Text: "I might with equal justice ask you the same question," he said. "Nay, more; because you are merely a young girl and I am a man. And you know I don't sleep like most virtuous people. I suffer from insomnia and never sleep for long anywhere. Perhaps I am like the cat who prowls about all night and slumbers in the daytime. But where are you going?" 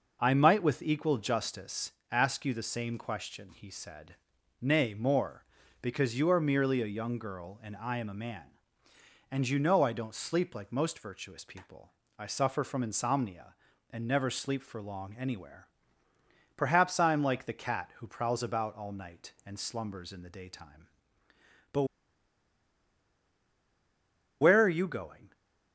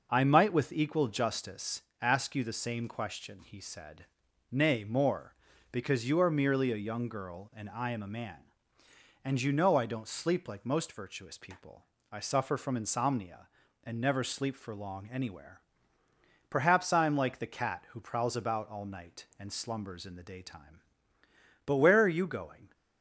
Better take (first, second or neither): second